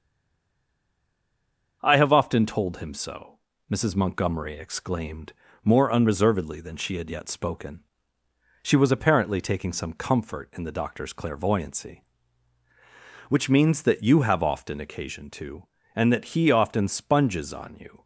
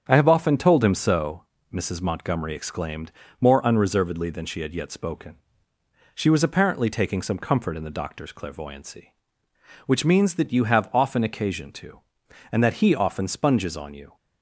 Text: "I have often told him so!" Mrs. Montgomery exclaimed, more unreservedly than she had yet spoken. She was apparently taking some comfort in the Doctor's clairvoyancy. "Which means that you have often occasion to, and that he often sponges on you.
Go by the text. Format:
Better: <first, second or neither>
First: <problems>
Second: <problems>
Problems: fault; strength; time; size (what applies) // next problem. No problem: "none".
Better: second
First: stays silent before the first word; noticeable; until 1.8 s; 1.8 s long // starts louder than the rest; until 2.8 s; 6 dB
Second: starts louder than the rest; strong; until 1.0 s; 7.5 dB